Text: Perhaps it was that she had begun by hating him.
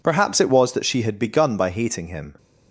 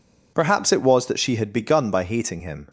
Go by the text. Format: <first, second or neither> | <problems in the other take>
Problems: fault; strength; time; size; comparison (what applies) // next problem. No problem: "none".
neither | none